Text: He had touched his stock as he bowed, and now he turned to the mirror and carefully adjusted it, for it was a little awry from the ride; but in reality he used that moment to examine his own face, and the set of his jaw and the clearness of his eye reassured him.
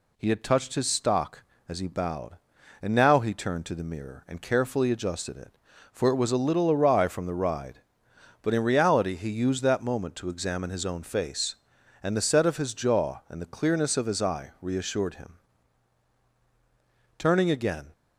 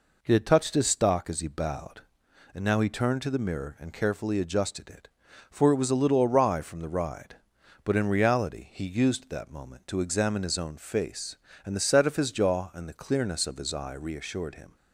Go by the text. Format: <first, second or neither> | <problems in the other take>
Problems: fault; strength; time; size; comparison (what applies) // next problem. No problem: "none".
second | goes on to say "Turning again"; noticeable; from 17.1 s on; 0.74 s long